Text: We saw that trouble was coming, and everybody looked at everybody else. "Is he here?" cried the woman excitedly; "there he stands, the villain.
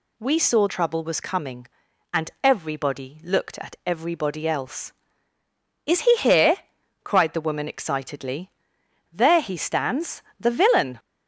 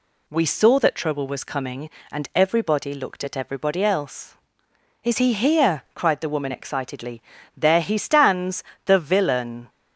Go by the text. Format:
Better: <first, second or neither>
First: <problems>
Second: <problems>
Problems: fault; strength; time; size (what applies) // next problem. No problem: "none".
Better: second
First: skips "that"; at 0.6 s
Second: none